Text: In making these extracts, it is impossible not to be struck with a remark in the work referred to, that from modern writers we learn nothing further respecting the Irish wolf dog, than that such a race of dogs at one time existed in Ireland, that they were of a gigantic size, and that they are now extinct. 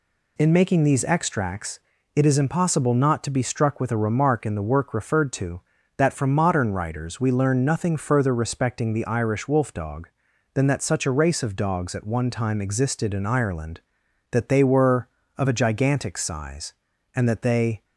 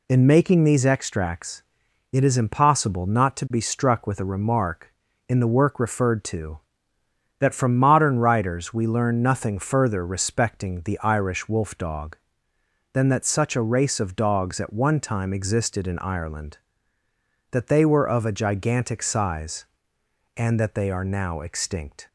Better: second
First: stops before "are now extinct"; at 17.8 s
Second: none

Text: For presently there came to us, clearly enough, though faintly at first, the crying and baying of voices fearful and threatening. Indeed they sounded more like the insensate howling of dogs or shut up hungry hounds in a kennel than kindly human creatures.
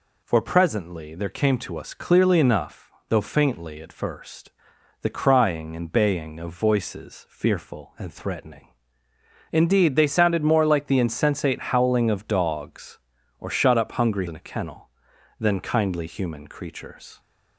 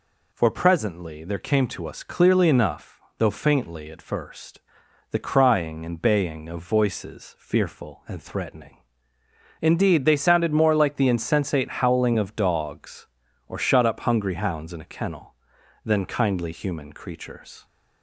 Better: second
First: skips "hounds"; at 14.2 s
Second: none

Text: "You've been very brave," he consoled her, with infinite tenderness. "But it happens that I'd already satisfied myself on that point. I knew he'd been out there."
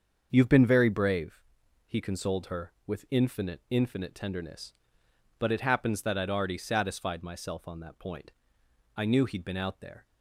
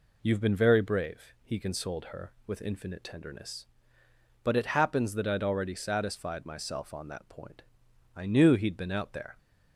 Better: second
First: starts louder than the rest; until 1.3 s; 7 dB // says "infinite" twice; at 3.6 s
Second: none

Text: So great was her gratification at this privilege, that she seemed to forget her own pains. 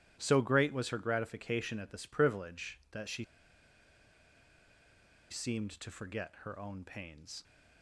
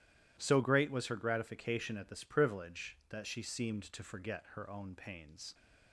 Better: second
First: pauses between "she" and "seemed"; strong; at 3.2 s; 2.0 s long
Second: none

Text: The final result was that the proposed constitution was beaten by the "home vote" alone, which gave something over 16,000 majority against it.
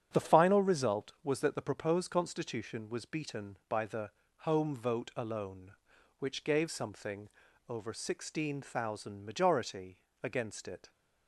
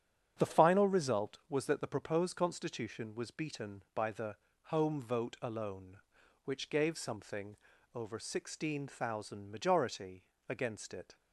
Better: neither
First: starts louder than the rest; strong; until 1.1 s; 8.5 dB // pauses between "the" and "home"; slight; at 4.0 s; 0.30 s long // pauses between "something" and "over"; at 7.2 s; 0.40 s long // pauses between "majority" and "against"; slight; at 9.9 s; 0.26 s long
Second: starts louder than the rest; strong; until 1.3 s; 8.5 dB // pauses between "the" and "home"; slight; at 4.3 s; 0.30 s long // pauses between "something" and "over"; at 7.5 s; 0.38 s long // pauses between "majority" and "against"; slight; at 10.2 s; 0.26 s long

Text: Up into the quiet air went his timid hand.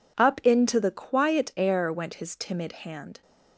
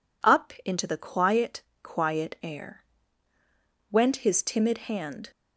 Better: first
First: none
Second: says "quiet" twice; at 1.8 s // pauses between "air" and "went"; at 2.8 s; 1.0 s long

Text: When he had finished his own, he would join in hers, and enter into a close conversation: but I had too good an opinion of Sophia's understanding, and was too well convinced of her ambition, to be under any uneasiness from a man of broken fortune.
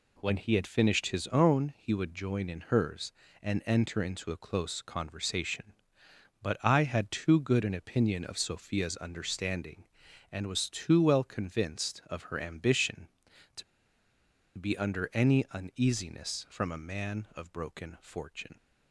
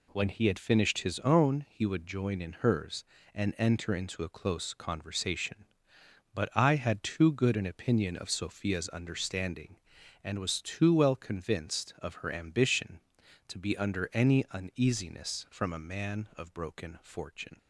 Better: second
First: pauses between "to" and "be"; noticeable; at 13.6 s; 0.95 s long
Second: none

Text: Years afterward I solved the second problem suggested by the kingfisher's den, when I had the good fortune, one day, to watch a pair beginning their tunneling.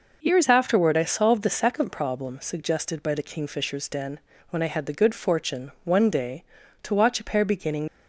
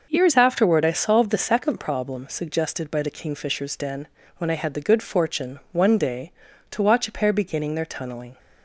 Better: second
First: stops before "their tunneling"; at 7.8 s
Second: none

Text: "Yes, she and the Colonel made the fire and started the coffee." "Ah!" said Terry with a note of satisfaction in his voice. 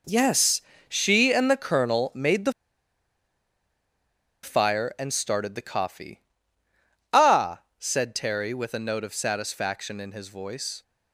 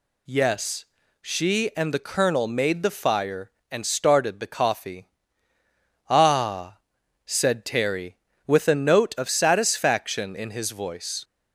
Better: second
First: pauses between "the" and "fire"; strong; at 2.5 s; 1.9 s long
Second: none

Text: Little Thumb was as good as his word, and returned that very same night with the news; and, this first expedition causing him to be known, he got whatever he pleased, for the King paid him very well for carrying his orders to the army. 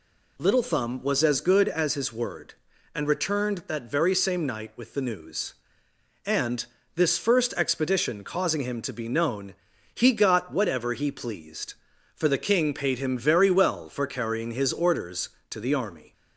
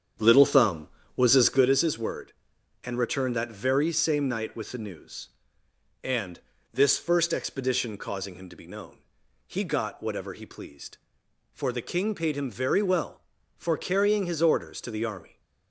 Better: first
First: none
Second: starts louder than the rest; strong; until 1.7 s; 8.5 dB

